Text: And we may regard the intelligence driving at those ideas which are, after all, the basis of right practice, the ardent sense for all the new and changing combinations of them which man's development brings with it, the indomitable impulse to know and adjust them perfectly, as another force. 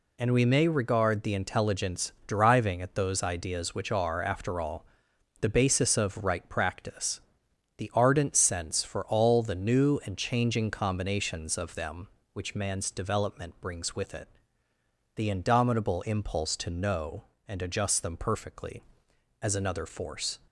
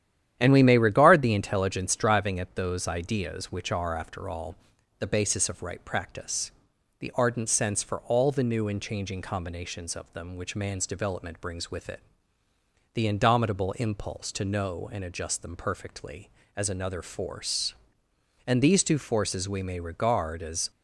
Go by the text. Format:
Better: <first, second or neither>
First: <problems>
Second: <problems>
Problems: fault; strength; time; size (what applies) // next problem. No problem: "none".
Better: first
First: none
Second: starts louder than the rest; strong; until 1.4 s; 10.5 dB // goes on to say "And these two forces we may regard as"; strong; from 18.4 s on; 2.2 s long